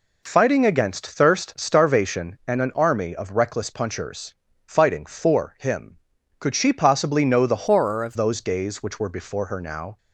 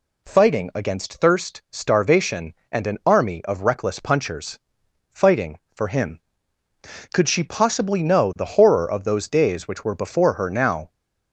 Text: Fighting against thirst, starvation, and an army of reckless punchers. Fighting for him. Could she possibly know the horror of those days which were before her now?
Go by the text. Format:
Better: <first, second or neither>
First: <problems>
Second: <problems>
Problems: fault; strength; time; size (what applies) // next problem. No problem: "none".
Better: second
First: changes voice from "horror" to "of"; from 7.6 to 8.1 s; 0.5 s long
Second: none